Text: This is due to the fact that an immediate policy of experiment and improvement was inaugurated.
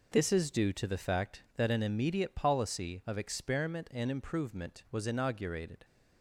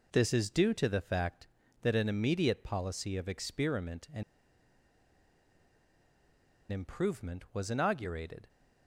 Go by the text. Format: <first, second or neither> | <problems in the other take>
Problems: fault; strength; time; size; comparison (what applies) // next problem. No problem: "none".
first | pauses between "and" and "improvement"; strong; at 4.2 s; 2.4 s long